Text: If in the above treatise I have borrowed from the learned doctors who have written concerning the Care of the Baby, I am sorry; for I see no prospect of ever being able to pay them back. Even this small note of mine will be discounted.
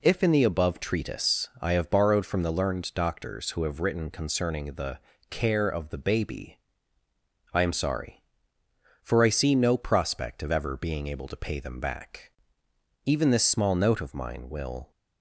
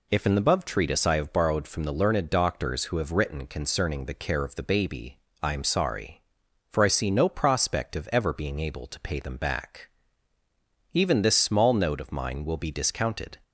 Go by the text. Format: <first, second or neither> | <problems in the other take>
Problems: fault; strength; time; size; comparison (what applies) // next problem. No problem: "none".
second | pauses between "the" and "Care"; slight; at 4.9 s; 0.30 s long // stops before "be discounted"; at 14.9 s